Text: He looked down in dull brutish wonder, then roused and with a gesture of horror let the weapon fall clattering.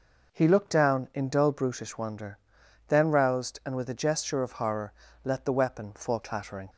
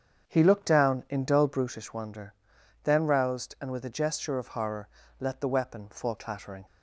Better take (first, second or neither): first